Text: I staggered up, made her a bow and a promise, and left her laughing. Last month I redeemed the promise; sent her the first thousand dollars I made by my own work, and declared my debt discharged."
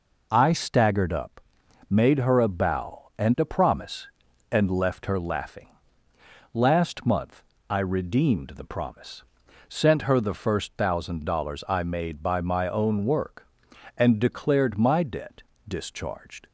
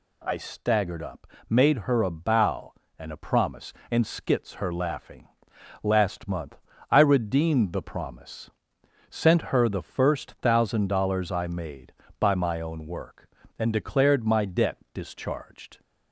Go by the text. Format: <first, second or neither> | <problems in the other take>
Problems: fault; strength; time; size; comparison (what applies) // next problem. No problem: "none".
first | says "skits" for "left"; at 4.0 s // pauses between "month" and "I"; slight; at 6.5 s; 0.32 s long; slight in the first // pauses between "debt" and "discharged"; slight; at 14.7 s; 0.16 s long; slight in the first